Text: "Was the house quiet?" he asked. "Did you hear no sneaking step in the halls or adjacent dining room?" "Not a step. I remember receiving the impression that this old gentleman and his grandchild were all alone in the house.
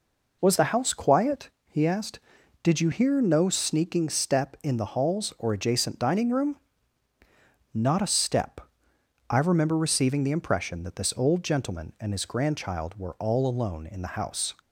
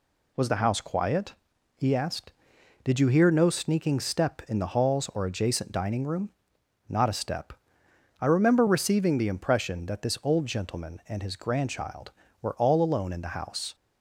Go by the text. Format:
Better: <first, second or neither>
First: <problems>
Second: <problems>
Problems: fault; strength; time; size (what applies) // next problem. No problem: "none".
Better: neither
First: none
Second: none